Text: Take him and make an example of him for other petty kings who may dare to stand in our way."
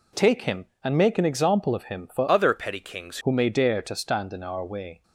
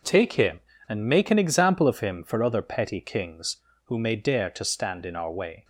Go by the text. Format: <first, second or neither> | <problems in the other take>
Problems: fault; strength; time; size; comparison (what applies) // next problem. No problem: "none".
second | changes voice from "other" to "kings"; from 2.2 to 3.1 s; 0.9 s long